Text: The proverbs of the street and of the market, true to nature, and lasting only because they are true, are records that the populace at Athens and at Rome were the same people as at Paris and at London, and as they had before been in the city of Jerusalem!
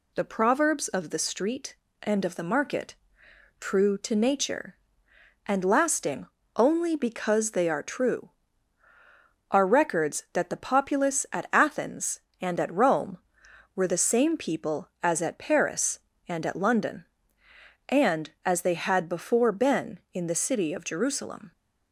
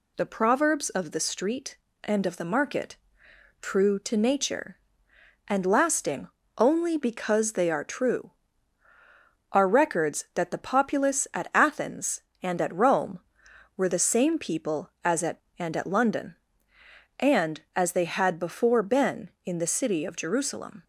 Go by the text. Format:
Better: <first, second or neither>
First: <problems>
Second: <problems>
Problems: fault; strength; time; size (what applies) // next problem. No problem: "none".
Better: first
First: pauses between "lasting" and "only"; slight; at 6.2 s; 0.28 s long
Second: pauses between "lasting" and "only"; slight; at 6.2 s; 0.28 s long // skips "Paris"; at 15.4 s